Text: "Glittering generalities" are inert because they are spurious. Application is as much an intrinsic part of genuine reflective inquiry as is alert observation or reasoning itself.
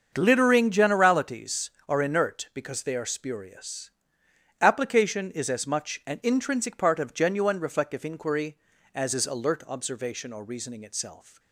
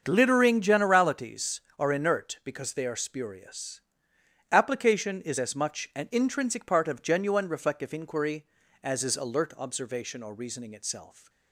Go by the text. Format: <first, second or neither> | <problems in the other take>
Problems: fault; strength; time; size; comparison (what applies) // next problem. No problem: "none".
neither | starts louder than the rest; the same in both